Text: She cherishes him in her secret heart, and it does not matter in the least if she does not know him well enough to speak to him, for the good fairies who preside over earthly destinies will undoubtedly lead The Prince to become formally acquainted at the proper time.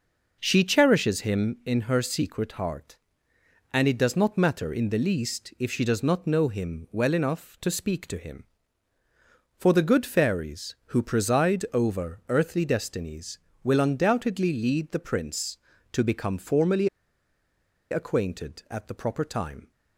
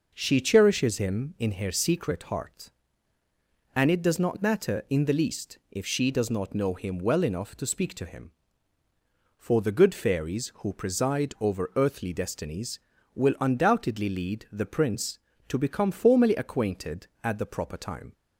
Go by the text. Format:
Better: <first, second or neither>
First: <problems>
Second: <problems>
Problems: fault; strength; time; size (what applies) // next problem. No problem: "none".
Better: second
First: pauses between "formally" and "acquainted"; at 16.8 s; 1.0 s long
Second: none